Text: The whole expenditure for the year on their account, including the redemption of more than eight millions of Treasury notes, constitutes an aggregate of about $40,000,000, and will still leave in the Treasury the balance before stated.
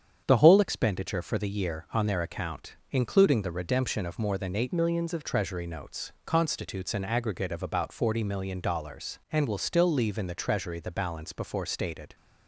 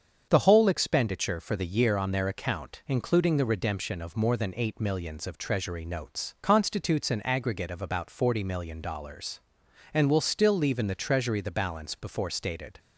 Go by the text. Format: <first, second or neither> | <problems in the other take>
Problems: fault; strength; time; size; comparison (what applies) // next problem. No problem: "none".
second | starts louder than the rest; strong; until 1.2 s; 8 dB; strong in the second // changes voice from "millions" to "of"; from 4.7 to 5.2 s; 0.5 s long